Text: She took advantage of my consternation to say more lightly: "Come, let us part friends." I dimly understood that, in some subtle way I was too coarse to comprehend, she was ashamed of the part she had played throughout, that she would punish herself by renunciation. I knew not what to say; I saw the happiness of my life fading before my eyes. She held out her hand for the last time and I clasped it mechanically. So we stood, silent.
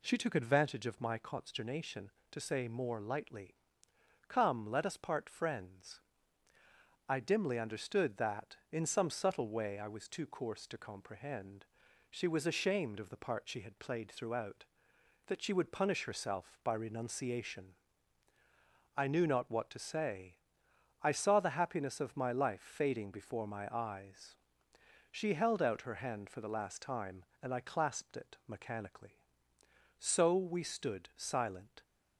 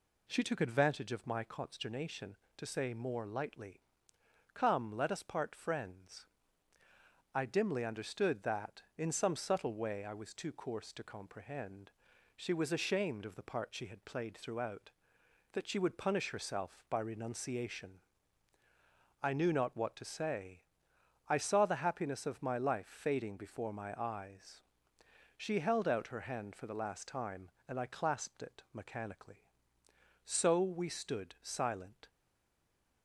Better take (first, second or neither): first